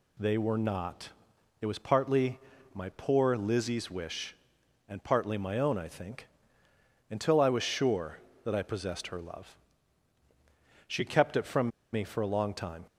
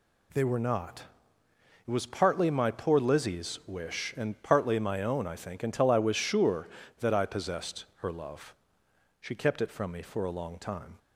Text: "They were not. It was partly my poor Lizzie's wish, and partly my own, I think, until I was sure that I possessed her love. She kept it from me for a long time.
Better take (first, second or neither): second